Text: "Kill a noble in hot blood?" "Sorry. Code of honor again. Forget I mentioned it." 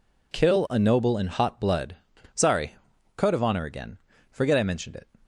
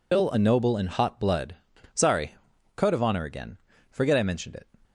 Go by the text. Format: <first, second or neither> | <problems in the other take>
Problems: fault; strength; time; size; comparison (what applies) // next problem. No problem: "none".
first | loses the start of "Kill"; at 0.1 s; 155 ms